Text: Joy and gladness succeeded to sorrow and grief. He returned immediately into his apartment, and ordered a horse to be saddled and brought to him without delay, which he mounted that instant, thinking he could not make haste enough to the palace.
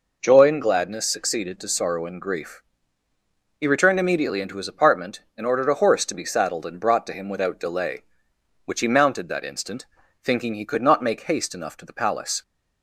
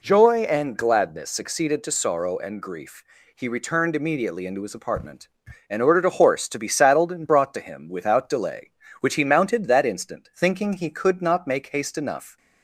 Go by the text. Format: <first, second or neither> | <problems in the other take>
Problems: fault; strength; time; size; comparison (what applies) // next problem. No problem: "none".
first | stops before "to the palace"; at 12.3 s